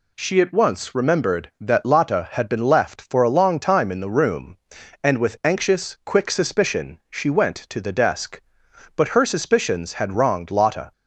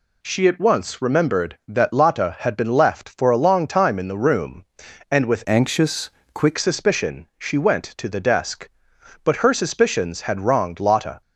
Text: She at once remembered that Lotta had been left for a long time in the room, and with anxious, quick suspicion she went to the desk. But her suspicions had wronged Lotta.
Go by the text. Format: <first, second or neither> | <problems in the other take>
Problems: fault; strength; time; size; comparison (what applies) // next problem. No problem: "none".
first | changes voice from "anxious" to "quick"; from 5.4 to 6.5 s; 1.1 s long